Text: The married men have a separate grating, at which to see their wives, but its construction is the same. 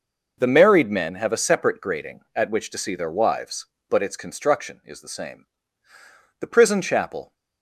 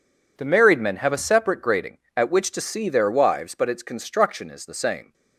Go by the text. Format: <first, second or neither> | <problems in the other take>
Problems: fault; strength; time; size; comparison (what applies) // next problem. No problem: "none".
second | goes on to say "The prison chapel"; noticeable; from 6.3 s on; 0.94 s long